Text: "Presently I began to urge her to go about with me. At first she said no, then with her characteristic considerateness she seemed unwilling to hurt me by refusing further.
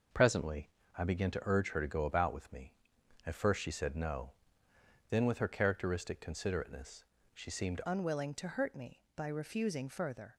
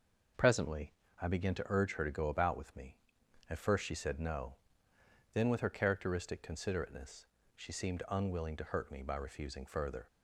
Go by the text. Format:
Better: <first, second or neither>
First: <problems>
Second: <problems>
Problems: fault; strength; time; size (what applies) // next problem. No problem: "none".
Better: second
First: pauses between "Presently" and "I"; slight; at 0.6 s; 0.28 s long // pauses between "considerateness" and "she"; slight; at 7.0 s; 0.28 s long // changes voice at "unwilling"; from 7.8 s on; 2.5 s long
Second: pauses between "Presently" and "I"; slight; at 0.9 s; 0.28 s long // pauses between "considerateness" and "she"; slight; at 7.2 s; 0.28 s long